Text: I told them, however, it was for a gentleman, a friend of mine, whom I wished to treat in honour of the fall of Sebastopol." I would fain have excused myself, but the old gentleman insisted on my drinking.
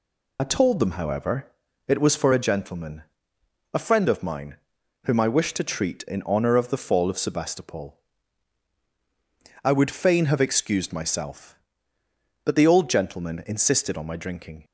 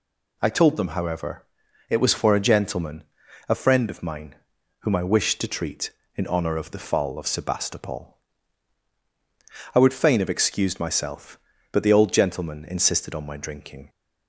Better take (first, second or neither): second